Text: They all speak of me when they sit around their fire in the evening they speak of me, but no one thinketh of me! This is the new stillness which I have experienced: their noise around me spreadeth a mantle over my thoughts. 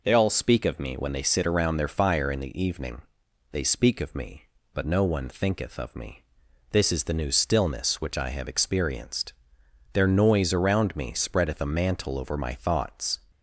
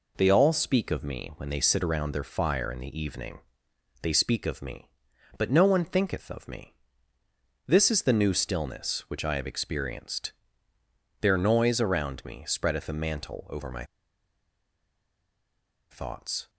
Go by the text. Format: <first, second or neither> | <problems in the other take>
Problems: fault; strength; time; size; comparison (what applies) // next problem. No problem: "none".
first | pauses between "evening" and "they"; noticeable; at 3.3 s; 0.62 s long; noticeable in the first // pauses between "my" and "thoughts"; strong; at 13.8 s; 2.0 s long